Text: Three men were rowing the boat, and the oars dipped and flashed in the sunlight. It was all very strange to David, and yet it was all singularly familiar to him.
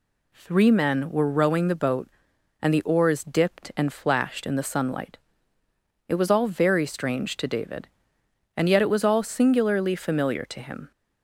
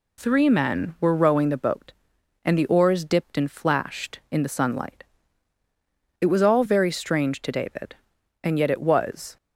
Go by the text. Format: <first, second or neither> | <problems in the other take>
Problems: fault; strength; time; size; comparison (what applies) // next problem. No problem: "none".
first | stops before "all singularly familiar to him"; at 9.3 s